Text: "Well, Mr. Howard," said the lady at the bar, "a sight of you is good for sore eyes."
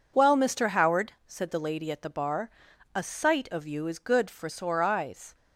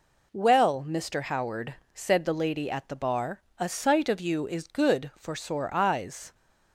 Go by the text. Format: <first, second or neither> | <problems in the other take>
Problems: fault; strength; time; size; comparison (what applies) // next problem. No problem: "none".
neither | none